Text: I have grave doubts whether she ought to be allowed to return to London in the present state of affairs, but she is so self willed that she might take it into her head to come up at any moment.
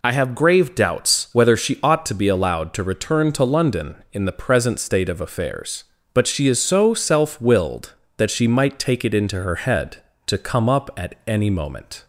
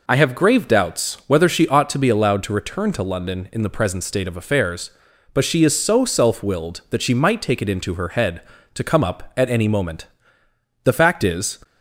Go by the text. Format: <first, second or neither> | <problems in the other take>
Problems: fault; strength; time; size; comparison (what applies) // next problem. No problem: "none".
first | goes on to say "The fact is"; noticeable; from 10.8 s on; 0.74 s long